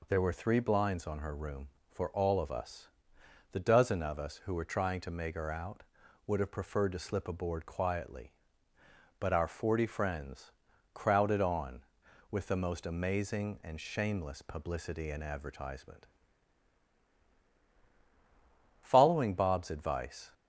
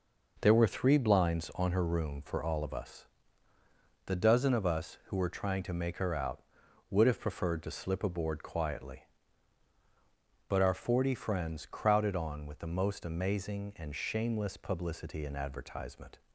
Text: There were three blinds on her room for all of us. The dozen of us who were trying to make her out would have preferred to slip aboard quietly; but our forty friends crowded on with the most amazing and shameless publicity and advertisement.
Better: second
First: pauses between "friends" and "crowded"; at 10.5 s; 0.42 s long // goes on to say "Following Bob's advice"; from 18.8 s on; 1.5 s long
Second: none

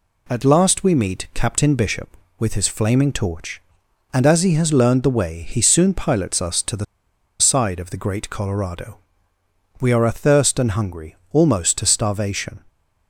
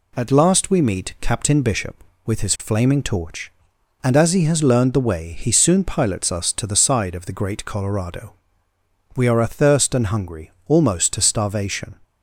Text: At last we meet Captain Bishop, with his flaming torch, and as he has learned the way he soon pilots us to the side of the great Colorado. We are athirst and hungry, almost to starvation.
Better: second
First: pauses between "the" and "side"; noticeable; at 6.8 s; 0.55 s long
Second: none

